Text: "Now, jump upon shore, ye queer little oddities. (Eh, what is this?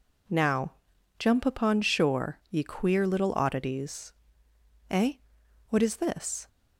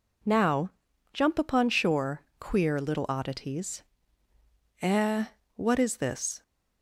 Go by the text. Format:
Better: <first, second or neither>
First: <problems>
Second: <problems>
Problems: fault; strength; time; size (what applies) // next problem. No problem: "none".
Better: first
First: none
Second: skips "ye"; at 2.3 s